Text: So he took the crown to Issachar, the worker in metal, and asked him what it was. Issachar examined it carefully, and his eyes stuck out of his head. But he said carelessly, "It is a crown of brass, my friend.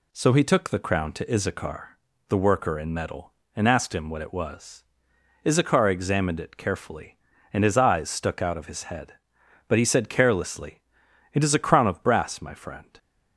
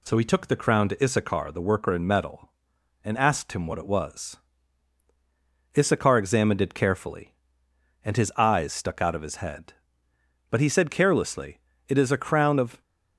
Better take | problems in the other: first | stops before "brass my friend"; at 12.8 s

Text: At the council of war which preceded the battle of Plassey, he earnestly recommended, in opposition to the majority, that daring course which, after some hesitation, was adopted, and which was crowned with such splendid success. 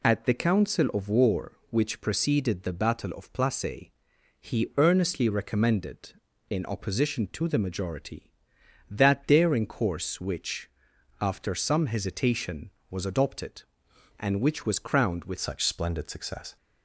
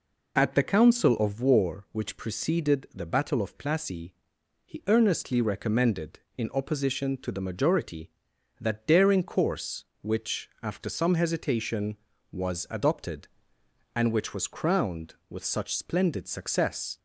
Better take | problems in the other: second | changes voice at "such"; from 15.3 s on; 1.2 s long

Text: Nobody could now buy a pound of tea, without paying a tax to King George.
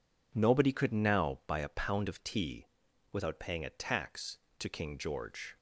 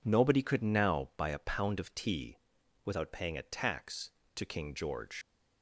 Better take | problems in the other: first | leaves "George" unfinished; at 5.2 s; 115 ms

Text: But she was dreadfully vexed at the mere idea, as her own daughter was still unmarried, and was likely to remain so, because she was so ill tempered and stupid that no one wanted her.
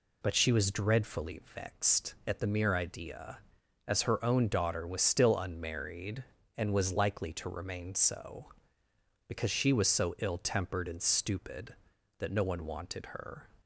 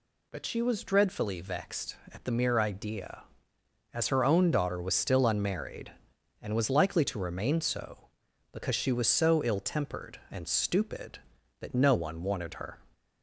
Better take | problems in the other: neither | none

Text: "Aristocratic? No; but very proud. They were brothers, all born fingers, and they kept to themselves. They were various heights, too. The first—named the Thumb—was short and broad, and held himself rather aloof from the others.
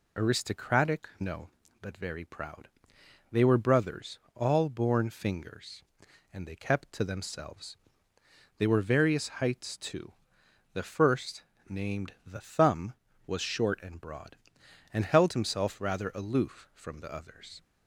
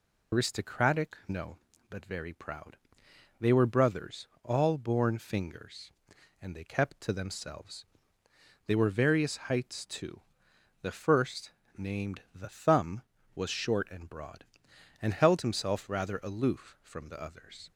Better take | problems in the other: first | loses the start of "Aristocratic"; at 0.3 s; 75 ms

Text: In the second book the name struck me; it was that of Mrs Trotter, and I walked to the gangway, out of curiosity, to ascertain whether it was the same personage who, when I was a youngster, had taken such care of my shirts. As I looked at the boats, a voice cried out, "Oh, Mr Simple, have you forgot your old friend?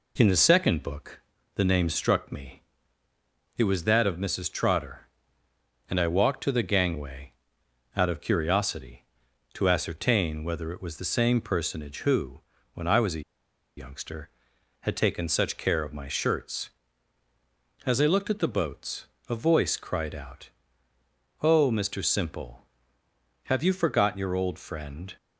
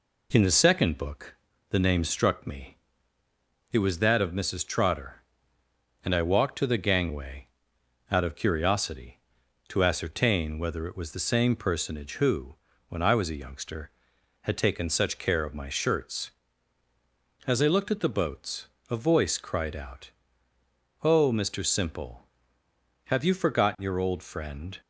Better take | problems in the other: second | pauses between "book" and "the"; slight; at 1.2 s; 0.36 s long; slight in the second // pauses between "a" and "youngster"; noticeable; at 13.2 s; 0.54 s long

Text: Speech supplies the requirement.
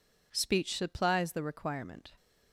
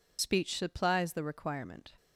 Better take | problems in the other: first | loses the start of "Speech"; at 0.1 s; 65 ms

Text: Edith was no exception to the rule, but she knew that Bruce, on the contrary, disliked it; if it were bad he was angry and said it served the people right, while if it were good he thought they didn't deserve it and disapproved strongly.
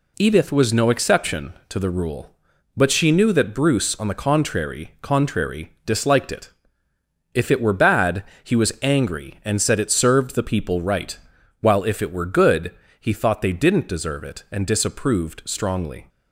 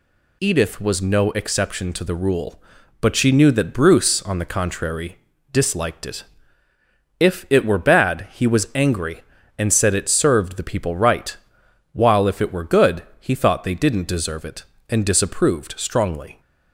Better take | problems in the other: second | says "contrary" twice; at 5.0 s // pauses between "bad" and "he"; slight; at 8.2 s; 0.22 s long // pauses between "good" and "he"; slight; at 12.7 s; 0.26 s long; slight in the second

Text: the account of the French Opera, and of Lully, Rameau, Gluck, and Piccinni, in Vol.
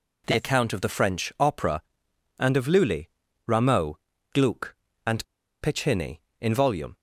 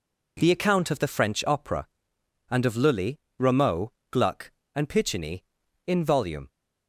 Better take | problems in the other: second | pauses between "and" and "Piccinni"; at 5.2 s; 0.38 s long

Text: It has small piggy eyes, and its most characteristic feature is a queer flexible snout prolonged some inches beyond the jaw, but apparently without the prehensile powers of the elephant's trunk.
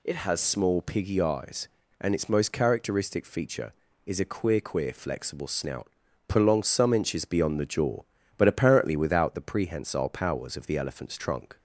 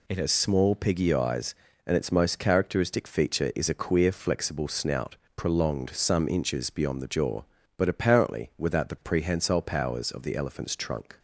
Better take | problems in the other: second | says "queer" twice; at 4.6 s // pauses between "snout" and "prolonged"; at 5.8 s; 0.40 s long; slight in the second

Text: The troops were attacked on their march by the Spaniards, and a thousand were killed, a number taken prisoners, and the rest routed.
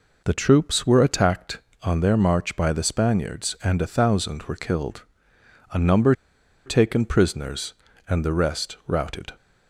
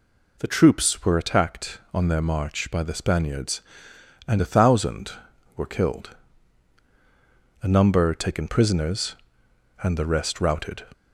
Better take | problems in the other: second | pauses between "number" and "taken"; noticeable; at 6.1 s; 0.53 s long

